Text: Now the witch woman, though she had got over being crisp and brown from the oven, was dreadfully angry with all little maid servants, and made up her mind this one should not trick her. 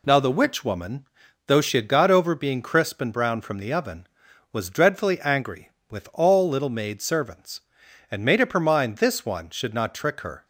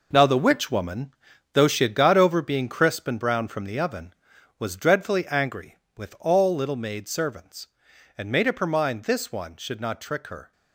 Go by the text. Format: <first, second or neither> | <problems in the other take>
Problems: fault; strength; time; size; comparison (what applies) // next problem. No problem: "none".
first | gets quieter; strong; throughout; 9.5 dB